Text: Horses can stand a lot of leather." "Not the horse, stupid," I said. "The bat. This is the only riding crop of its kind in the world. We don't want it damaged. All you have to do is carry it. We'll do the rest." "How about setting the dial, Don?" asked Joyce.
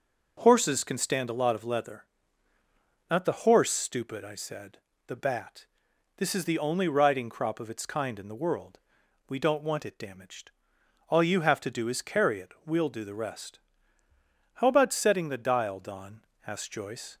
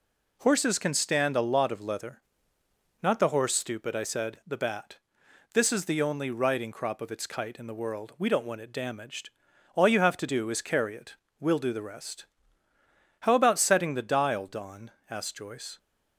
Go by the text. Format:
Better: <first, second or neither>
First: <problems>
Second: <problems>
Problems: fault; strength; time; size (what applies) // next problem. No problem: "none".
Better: first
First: none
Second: says "kite" for "kind"; at 7.2 s